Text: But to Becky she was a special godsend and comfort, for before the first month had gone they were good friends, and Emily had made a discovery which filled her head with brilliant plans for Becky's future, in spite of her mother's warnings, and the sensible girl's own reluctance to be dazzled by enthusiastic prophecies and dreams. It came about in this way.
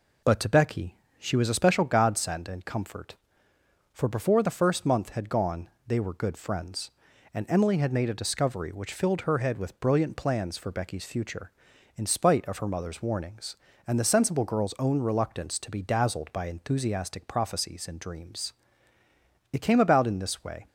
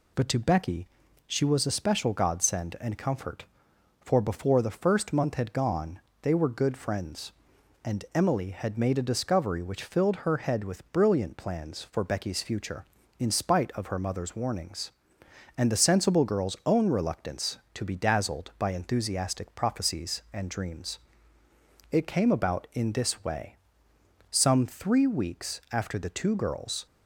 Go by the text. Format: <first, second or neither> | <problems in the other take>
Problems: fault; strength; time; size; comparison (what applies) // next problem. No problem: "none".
first | pauses between "Becky" and "she"; at 0.8 s; 0.38 s long; slight in the first // pauses between "gone" and "they"; slight; at 5.9 s; 0.22 s long; slight in the first // goes on to say "Some three weeks after the two girls"; strong; from 24.2 s on; 2.5 s long